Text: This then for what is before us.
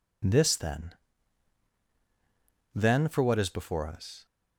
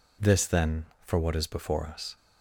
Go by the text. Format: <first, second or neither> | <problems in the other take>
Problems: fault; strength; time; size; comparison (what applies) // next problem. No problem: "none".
second | says "then" twice; at 2.7 s